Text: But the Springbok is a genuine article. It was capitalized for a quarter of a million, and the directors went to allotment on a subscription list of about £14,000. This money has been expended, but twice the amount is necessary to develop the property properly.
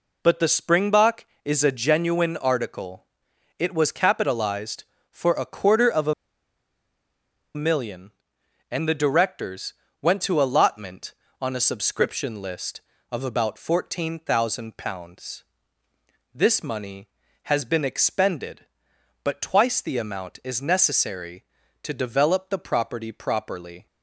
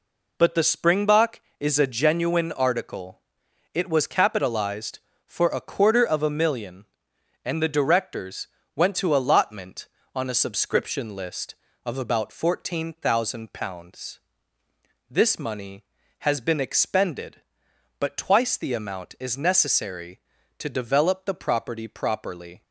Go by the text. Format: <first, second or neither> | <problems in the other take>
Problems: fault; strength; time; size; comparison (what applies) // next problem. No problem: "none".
second | pauses between "a" and "million"; strong; at 6.1 s; 1.4 s long // pauses between "directors" and "went"; slight; at 9.7 s; 0.28 s long; slight in the second